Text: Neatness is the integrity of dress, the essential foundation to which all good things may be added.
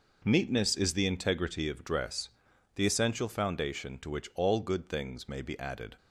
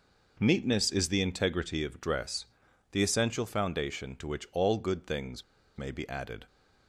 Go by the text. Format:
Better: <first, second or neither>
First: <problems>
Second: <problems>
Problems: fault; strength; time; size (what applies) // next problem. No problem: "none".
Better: first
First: none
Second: pauses between "things" and "may"; slight; at 5.4 s; 0.32 s long